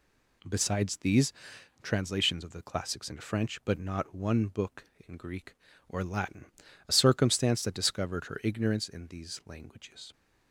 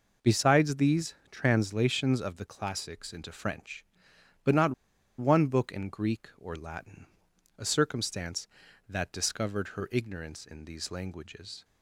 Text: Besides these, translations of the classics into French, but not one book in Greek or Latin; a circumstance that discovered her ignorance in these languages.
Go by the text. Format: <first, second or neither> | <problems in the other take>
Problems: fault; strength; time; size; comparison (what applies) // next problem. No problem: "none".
first | pauses between "not" and "one"; noticeable; at 4.7 s; 0.46 s long